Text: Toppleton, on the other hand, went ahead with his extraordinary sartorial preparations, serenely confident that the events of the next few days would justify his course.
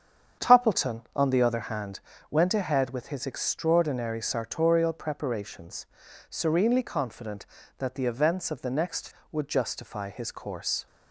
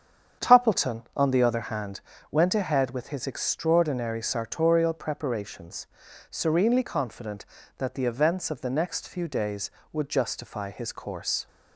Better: second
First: starts louder than the rest; strong; until 1.5 s; 8 dB // skips "few days"; at 9.1 s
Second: starts louder than the rest; strong; until 1.5 s; 8 dB

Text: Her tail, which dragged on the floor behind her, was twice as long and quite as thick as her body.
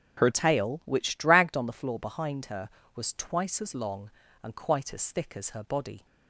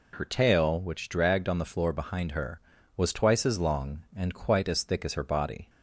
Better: second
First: starts louder than the rest; until 1.2 s; 7 dB // changes voice at "tail"; from 0.3 s on; 5.7 s long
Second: none

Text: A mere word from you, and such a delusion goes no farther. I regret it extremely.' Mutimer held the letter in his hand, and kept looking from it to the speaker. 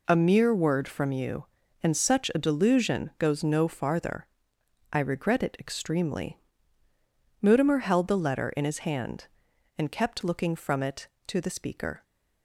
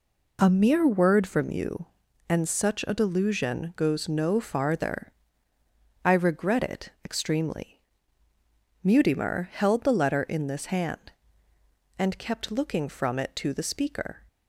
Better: first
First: none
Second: says "this" for "his"; at 10.4 s

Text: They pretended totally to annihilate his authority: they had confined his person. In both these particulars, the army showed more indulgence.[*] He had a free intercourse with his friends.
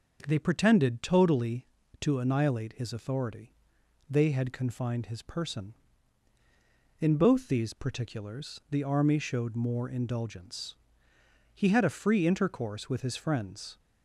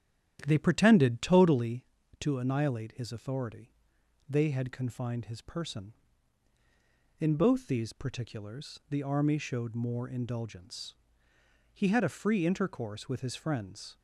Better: first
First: none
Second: starts louder than the rest; strong; until 1.8 s; 10 dB

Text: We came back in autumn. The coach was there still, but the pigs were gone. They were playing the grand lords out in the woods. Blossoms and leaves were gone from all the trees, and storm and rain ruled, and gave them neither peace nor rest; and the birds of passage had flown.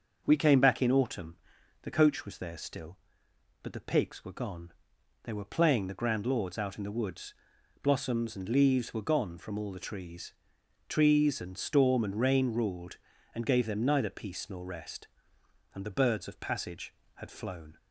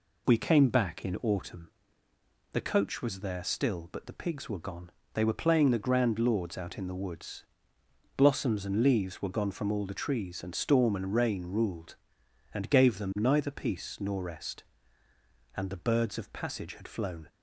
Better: second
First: starts louder than the rest; until 1.2 s; 6.5 dB // says "trees" twice; at 10.8 s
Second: none

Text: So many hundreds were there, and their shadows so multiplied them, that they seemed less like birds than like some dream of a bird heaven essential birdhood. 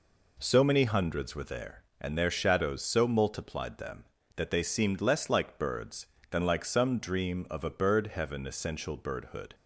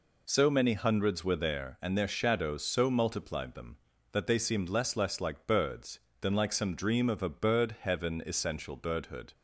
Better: first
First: none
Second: says "less" twice; at 4.9 s

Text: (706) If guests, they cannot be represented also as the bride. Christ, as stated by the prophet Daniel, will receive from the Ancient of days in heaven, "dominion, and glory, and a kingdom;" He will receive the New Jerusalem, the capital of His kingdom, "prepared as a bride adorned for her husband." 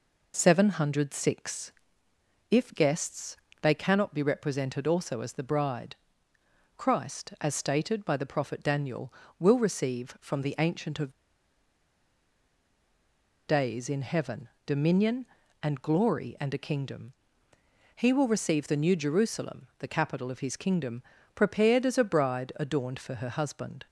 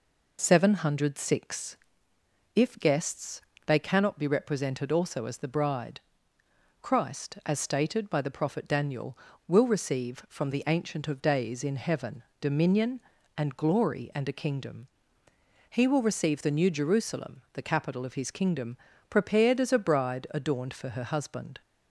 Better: second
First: pauses between "of" and "days"; strong; at 11.1 s; 2.3 s long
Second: none

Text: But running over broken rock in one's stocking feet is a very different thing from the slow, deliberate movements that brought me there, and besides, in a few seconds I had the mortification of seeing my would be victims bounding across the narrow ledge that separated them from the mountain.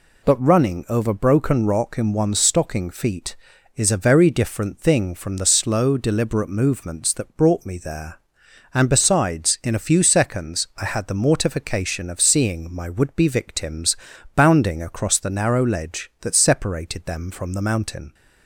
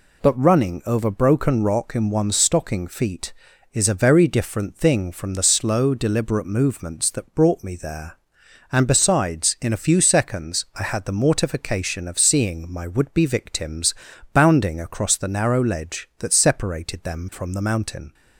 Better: neither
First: pauses between "victims" and "bounding"; at 13.9 s; 0.40 s long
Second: pauses between "victims" and "bounding"; at 13.9 s; 0.40 s long

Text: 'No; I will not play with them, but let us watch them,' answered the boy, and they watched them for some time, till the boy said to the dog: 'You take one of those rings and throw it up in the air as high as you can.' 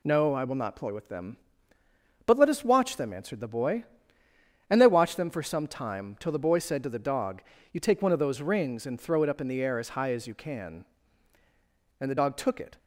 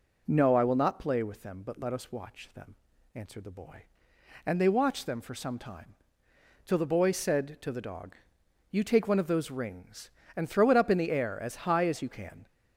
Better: second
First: goes on to say "And the dog took it"; noticeable; from 11.9 s on; 0.78 s long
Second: none

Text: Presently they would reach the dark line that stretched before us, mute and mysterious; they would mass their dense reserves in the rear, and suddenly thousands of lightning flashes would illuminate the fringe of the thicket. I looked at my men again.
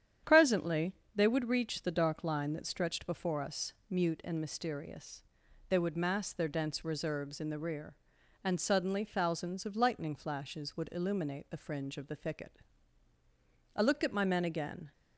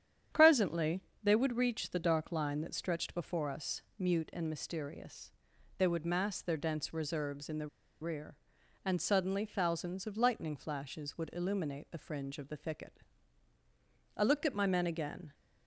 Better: first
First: starts louder than the rest; strong; until 1.4 s; 9 dB // pauses between "Presently" and "they"; slight; at 0.9 s; 0.22 s long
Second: starts louder than the rest; strong; until 1.5 s; 9 dB // pauses between "Presently" and "they"; slight; at 1.0 s; 0.22 s long // pauses between "the" and "rear"; slight; at 7.6 s; 0.34 s long

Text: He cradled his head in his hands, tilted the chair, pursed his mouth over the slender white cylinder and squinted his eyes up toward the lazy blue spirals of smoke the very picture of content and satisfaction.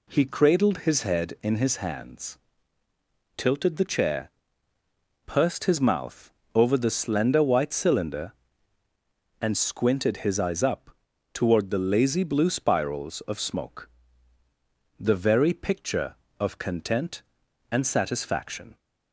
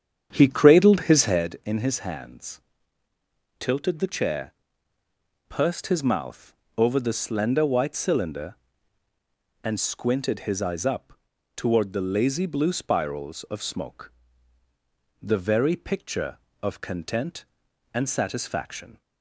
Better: first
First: pauses between "mouth" and "over"; slight; at 6.3 s; 0.24 s long // pauses between "up" and "toward"; noticeable; at 10.8 s; 0.46 s long // pauses between "smoke" and "the"; at 13.9 s; 1.0 s long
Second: starts louder than the rest; strong; until 1.4 s; 8.5 dB // pauses between "mouth" and "over"; slight; at 6.5 s; 0.24 s long // pauses between "up" and "toward"; noticeable; at 11.1 s; 0.46 s long // pauses between "smoke" and "the"; at 14.1 s; 1.0 s long

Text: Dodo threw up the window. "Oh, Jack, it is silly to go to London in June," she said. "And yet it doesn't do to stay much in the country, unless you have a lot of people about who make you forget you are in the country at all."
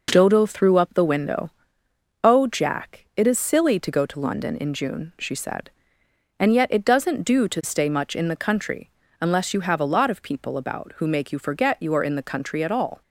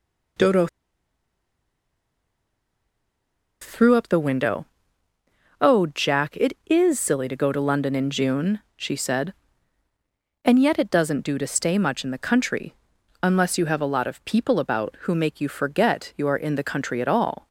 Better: first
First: none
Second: pauses between "Dodo" and "threw"; strong; at 0.6 s; 2.9 s long

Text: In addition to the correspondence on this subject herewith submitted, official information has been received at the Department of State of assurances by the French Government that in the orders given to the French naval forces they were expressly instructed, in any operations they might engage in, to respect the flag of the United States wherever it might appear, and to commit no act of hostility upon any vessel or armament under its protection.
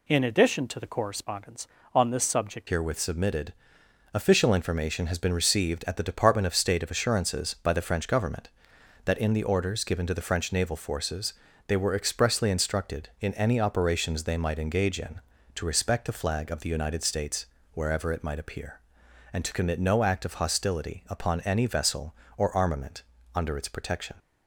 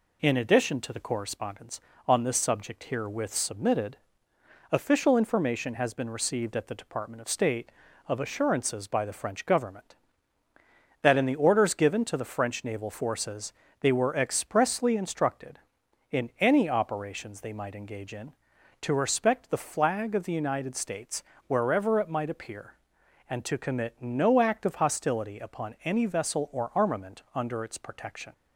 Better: second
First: changes voice at "herewith"; from 2.6 s on; 21.5 s long // pauses between "forces" and "they"; slight; at 11.3 s; 0.34 s long // pauses between "States" and "wherever"; slight; at 17.4 s; 0.28 s long // pauses between "armament" and "under"; slight; at 23.0 s; 0.32 s long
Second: pauses between "forces" and "they"; slight; at 13.5 s; 0.28 s long // pauses between "States" and "wherever"; slight; at 21.2 s; 0.24 s long

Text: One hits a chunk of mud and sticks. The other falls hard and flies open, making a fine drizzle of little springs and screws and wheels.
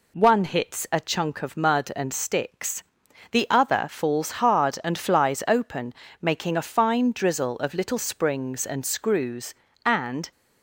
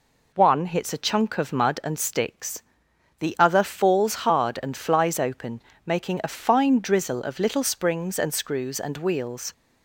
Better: second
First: stops before "wheels"; at 10.3 s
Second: none

